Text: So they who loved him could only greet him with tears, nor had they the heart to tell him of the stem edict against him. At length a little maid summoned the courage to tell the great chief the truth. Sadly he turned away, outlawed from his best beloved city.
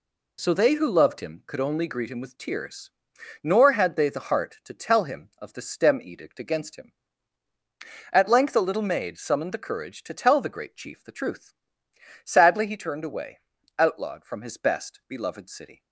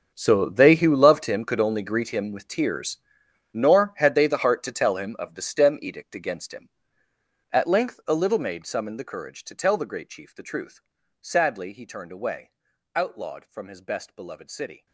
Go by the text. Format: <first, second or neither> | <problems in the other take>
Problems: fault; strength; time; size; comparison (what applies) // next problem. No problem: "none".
first | gets quieter; strong; throughout; 17 dB